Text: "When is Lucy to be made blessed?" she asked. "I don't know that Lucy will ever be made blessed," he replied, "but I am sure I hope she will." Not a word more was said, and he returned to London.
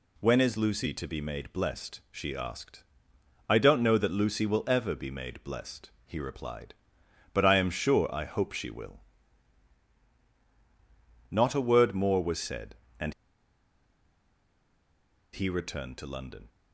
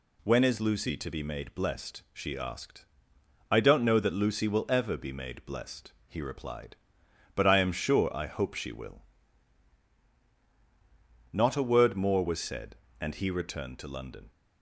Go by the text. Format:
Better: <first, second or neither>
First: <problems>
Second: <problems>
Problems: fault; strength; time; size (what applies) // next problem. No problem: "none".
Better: second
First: pauses between "and" and "he"; strong; at 13.1 s; 2.2 s long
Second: none